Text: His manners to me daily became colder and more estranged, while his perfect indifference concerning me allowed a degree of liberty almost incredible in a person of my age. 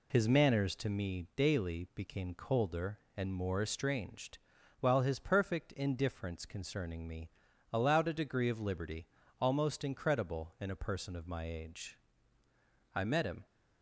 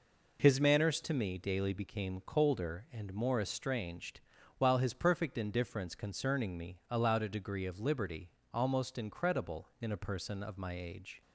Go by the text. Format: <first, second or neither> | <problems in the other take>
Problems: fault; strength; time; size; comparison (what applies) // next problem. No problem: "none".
second | pauses between "me" and "allowed"; at 7.2 s; 0.42 s long // pauses between "liberty" and "almost"; slight; at 9.0 s; 0.32 s long; slight in the second // goes on to say "I met him"; from 12.9 s on; 0.52 s long